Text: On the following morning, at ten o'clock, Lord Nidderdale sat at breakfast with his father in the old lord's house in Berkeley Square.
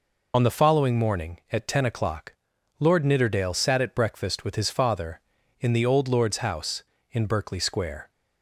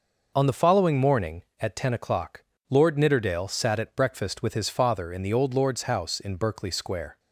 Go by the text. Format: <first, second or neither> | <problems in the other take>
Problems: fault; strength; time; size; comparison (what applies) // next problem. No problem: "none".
second | loses the start of "On"; at 0.3 s; 45 ms